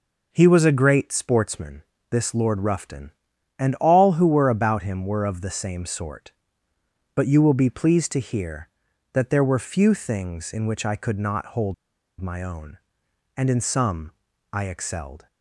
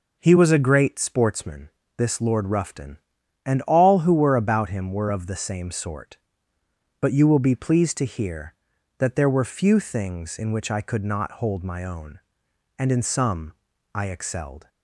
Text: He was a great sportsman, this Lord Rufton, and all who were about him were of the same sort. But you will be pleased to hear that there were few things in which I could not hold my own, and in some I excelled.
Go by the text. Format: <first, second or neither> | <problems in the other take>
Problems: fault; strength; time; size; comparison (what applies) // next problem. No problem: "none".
second | pauses between "hold" and "my"; noticeable; at 11.7 s; 0.46 s long // pauses between "some" and "I"; at 14.1 s; 0.40 s long; also in the second